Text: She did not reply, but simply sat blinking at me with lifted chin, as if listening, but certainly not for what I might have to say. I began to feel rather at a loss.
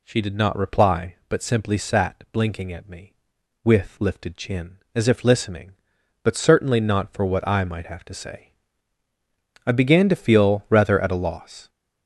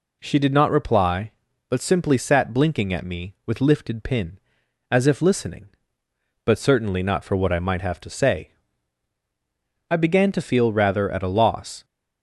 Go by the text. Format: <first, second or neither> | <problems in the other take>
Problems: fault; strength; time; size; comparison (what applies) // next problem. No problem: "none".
first | says "pin" for "chin"; at 4.0 s